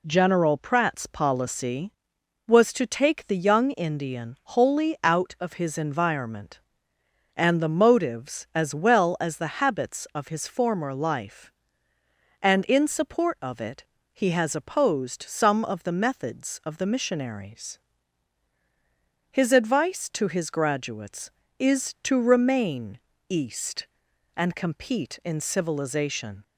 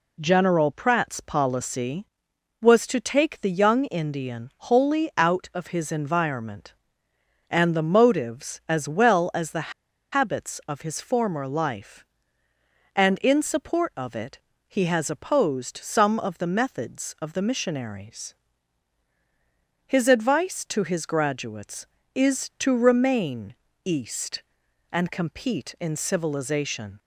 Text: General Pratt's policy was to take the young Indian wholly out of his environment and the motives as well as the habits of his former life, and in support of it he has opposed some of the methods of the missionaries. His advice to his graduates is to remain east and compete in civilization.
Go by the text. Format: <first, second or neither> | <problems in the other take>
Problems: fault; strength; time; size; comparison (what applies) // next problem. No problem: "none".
first | pauses between "the" and "habits"; at 9.7 s; 0.41 s long // pauses between "it" and "he"; slight; at 14.4 s; 0.26 s long; slight in the first // pauses between "remain" and "east"; slight; at 23.5 s; 0.30 s long; slight in the first